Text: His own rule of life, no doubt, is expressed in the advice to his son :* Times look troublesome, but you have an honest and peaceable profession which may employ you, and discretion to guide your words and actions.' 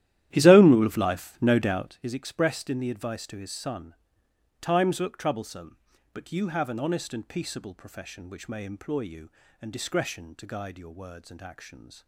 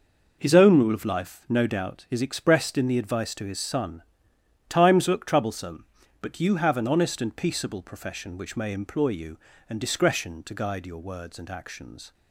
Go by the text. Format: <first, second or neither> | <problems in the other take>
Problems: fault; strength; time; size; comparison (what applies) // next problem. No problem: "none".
second | starts louder than the rest; strong; until 2.1 s; 13 dB